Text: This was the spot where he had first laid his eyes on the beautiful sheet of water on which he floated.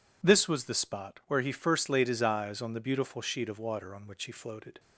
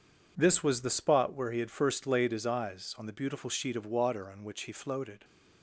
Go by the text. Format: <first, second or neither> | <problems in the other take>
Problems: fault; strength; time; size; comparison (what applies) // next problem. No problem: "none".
second | skips "had"; at 1.5 s